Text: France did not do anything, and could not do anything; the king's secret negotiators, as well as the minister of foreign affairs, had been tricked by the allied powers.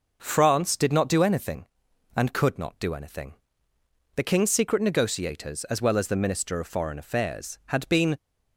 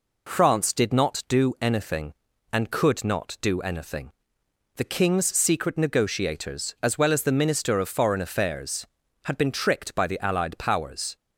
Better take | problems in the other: second | stops before "tricked by the allied powers"; at 8.1 s

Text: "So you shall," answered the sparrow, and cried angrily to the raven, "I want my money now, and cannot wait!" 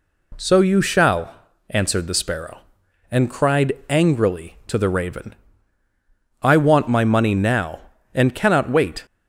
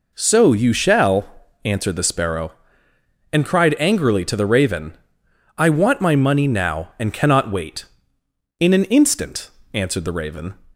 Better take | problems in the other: first | goes on to say "In an instant answered the raven"; strong; from 8.5 s on; 1.9 s long

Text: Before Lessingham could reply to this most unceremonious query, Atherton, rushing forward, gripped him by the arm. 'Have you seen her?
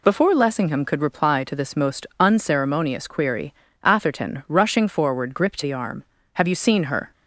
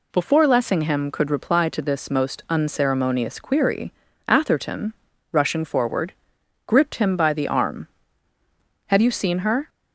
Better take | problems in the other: second | skips "him by"; at 5.6 s

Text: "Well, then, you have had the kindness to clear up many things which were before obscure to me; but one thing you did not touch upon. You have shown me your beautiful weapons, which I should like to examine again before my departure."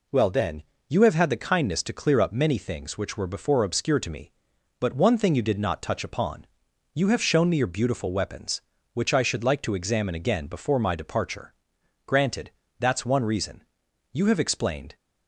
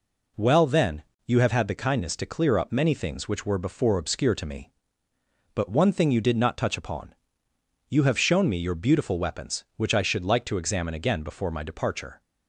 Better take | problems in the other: second | goes on to say "Granted That's one reason You have explained"; strong; from 12.0 s on; 2.8 s long

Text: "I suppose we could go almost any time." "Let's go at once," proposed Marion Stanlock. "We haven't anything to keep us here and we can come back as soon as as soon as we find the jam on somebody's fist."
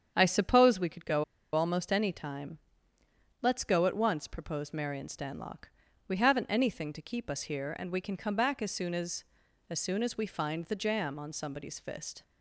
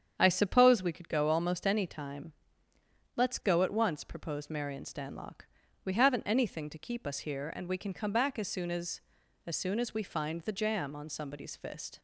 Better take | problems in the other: second | starts louder than the rest; strong; until 1.1 s; 8 dB; strong in the second // pauses between "go" and "almost"; slight; at 1.2 s; 0.30 s long

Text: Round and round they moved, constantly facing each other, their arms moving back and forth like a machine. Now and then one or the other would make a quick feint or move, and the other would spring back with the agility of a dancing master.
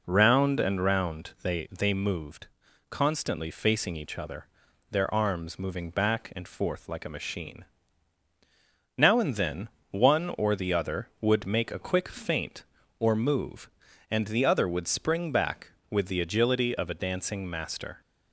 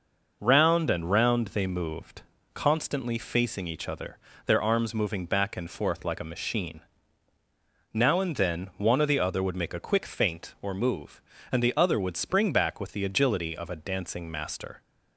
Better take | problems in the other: second | says "they" twice; at 1.7 s // pauses between "then" and "one"; slight; at 9.6 s; 0.22 s long

